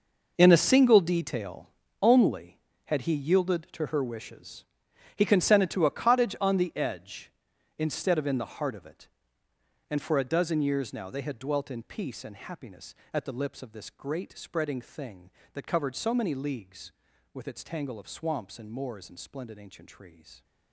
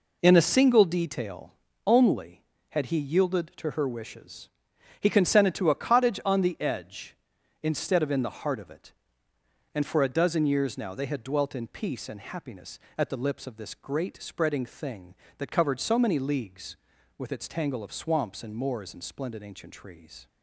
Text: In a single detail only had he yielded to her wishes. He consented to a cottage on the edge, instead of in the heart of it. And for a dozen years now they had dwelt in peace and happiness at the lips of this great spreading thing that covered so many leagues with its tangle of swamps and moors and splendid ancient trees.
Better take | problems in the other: second | gets quieter; strong; throughout; 14 dB // pauses between "detail" and "only"; slight; at 1.6 s; 0.32 s long; slight in the second

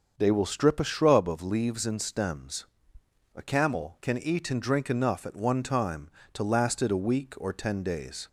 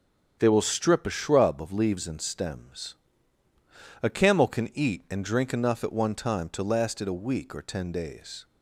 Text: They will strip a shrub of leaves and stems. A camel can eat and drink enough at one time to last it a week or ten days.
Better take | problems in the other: neither | starts louder than the rest; the same in both

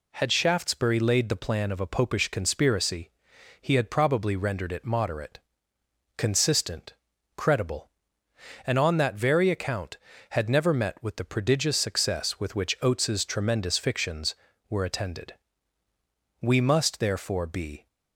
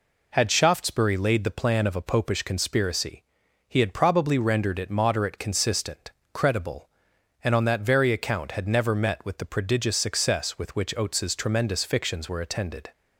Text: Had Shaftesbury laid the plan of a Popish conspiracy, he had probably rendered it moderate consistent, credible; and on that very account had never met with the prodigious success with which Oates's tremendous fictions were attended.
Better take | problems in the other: second | pauses between "moderate" and "consistent"; noticeable; at 5.3 s; 0.78 s long // goes on to say "We must therefore be"; from 16.4 s on; 1.4 s long

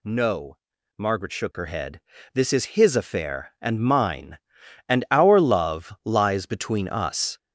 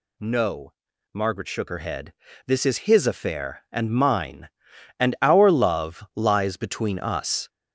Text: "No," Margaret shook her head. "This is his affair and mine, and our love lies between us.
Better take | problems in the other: neither | none

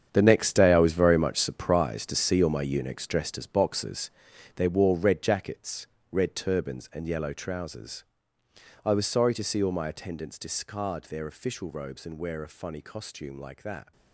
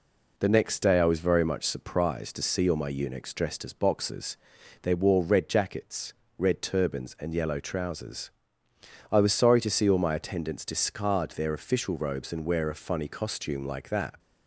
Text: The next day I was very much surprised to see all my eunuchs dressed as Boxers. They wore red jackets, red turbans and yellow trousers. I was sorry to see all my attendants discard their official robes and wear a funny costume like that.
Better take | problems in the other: second | gets quieter; strong; throughout; 13 dB

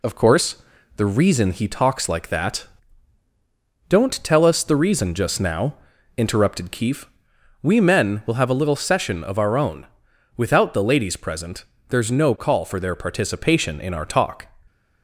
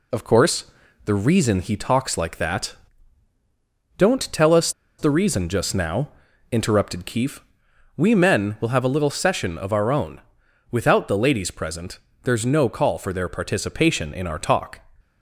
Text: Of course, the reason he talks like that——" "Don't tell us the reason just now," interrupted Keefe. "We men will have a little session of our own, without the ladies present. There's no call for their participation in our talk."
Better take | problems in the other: first | pauses between "us" and "the"; slight; at 4.7 s; 0.28 s long

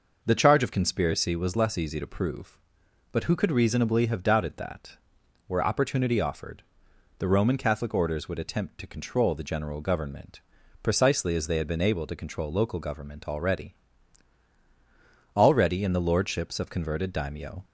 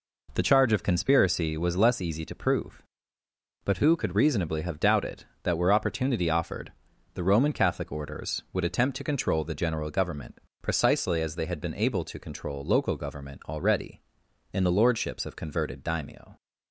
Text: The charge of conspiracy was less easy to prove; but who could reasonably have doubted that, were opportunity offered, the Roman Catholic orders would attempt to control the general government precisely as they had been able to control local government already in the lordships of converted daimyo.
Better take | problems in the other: second | pauses between "government" and "precisely"; at 10.4 s; 0.40 s long; slight in the second // says "already" twice; at 15.3 s

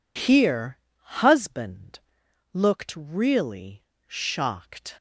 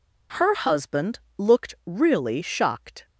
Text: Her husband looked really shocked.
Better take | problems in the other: second | says "Here" for "Her"; at 0.1 s // pauses between "husband" and "looked"; noticeable; at 1.9 s; 0.56 s long; slight in the second // pauses between "really" and "shocked"; slight; at 3.8 s; 0.24 s long

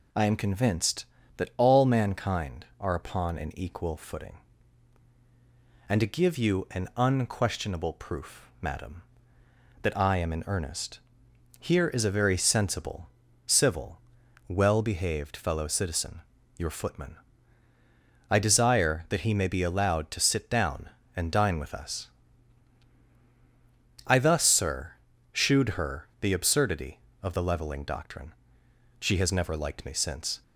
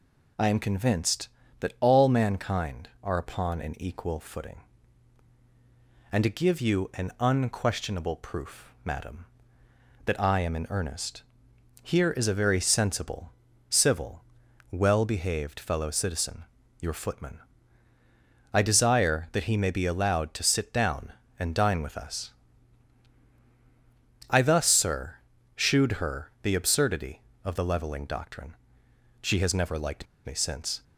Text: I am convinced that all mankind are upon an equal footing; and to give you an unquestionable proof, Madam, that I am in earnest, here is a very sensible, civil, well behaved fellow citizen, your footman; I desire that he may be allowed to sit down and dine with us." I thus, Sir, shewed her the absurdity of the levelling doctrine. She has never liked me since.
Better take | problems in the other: first | pauses between "liked" and "me"; slight; at 30.0 s; 0.19 s long

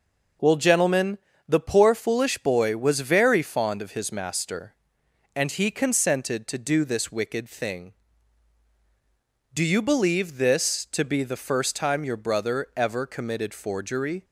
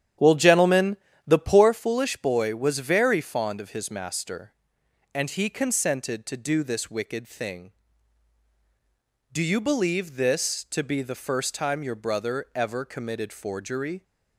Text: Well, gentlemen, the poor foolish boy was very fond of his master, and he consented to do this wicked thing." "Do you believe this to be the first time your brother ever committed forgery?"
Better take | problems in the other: first | starts louder than the rest; strong; until 1.7 s; 10 dB

